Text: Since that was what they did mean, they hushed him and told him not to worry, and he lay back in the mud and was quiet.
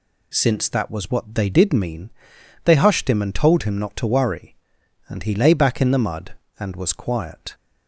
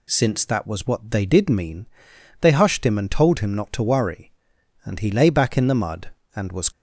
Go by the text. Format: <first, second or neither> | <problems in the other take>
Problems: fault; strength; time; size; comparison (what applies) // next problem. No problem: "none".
first | stops before "quiet"; at 6.7 s